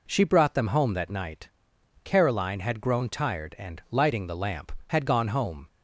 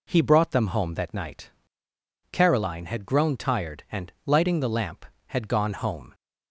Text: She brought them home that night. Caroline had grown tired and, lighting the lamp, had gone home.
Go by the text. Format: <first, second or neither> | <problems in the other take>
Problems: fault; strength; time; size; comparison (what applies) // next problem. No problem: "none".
first | says "He" for "She"; at 0.1 s